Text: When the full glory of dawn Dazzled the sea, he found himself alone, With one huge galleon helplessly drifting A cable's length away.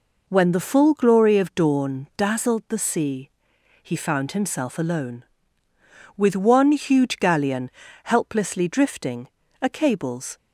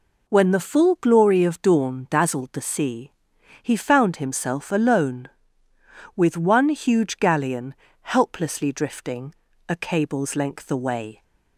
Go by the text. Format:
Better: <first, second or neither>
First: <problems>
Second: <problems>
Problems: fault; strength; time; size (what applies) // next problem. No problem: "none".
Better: second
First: pauses between "galleon" and "helplessly"; slight; at 7.7 s; 0.32 s long // pauses between "drifting" and "A"; slight; at 9.2 s; 0.34 s long // stops before "length away"; at 10.3 s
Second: pauses between "galleon" and "helplessly"; slight; at 7.7 s; 0.26 s long // pauses between "drifting" and "A"; slight; at 9.3 s; 0.34 s long